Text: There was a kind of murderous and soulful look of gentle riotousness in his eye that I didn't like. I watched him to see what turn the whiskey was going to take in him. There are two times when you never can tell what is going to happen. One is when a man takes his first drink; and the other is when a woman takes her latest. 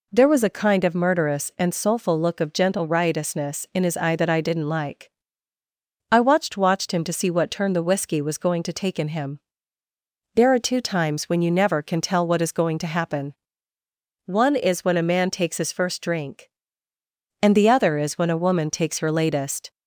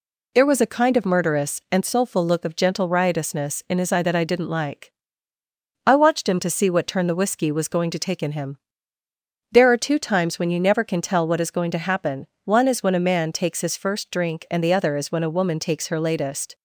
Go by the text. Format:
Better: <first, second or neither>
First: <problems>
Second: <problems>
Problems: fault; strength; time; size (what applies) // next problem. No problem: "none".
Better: second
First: says "watched" twice; at 6.5 s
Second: none